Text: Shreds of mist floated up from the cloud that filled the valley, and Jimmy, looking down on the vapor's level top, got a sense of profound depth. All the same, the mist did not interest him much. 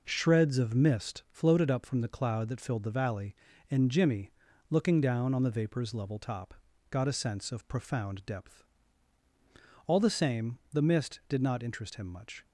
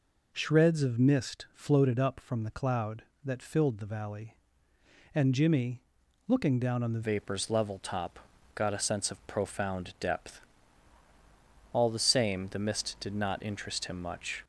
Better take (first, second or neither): first